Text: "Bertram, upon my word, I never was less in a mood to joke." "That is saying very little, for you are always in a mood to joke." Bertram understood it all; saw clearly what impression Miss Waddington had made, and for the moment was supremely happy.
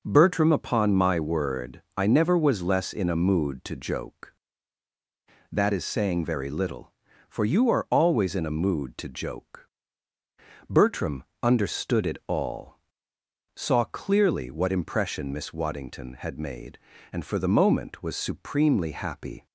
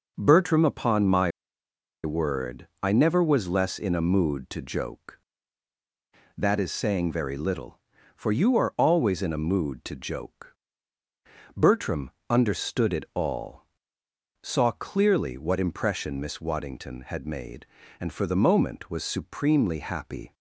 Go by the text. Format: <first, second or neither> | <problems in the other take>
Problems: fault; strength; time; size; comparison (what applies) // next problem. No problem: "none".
first | pauses between "my" and "word"; noticeable; at 1.3 s; 0.74 s long // pauses between "Bertram" and "understood"; slight; at 12.1 s; 0.18 s long; slight in the first